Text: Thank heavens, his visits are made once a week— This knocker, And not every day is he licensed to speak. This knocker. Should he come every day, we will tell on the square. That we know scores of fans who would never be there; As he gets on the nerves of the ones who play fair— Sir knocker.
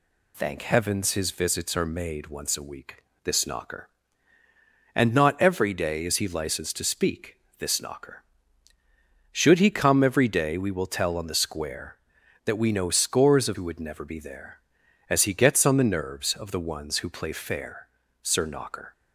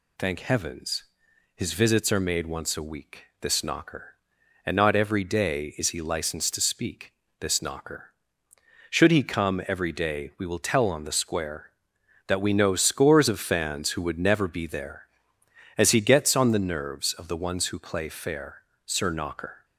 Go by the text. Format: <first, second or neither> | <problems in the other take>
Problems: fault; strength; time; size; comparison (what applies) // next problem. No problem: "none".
second | skips "fans"; at 13.5 s